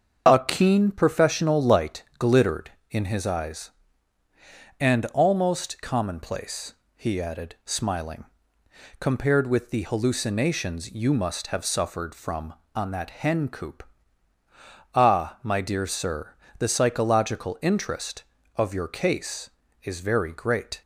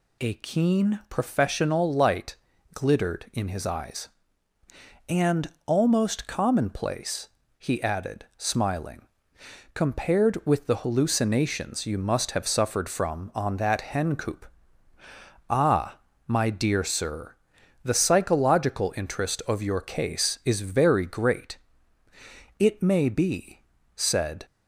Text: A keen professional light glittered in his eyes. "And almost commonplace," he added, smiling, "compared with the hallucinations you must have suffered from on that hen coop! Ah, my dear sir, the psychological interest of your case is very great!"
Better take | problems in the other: first | pauses between "light" and "glittered"; slight; at 2.3 s; 0.36 s long; slight in the first // pauses between "And" and "almost"; slight; at 5.5 s; 0.16 s long // goes on to say "It may be said"; strong; from 22.6 s on; 1.7 s long

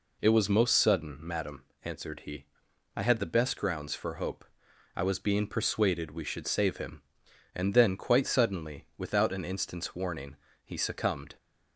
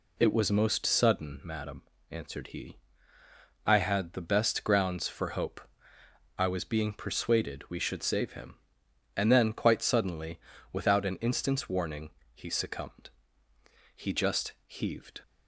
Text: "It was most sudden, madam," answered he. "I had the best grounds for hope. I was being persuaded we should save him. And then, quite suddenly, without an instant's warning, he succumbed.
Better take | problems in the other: first | goes on to say "He just heaved"; noticeable; from 13.9 s on; 1.2 s long

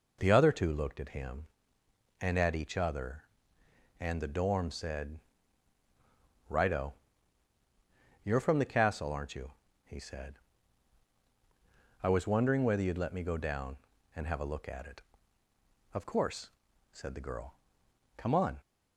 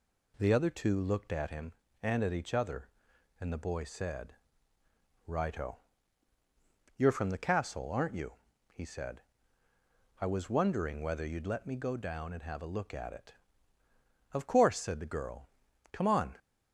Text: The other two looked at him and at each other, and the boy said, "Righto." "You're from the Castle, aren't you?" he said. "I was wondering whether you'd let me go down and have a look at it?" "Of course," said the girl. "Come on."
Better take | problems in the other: second | says "dorm" for "boy"; at 4.3 s

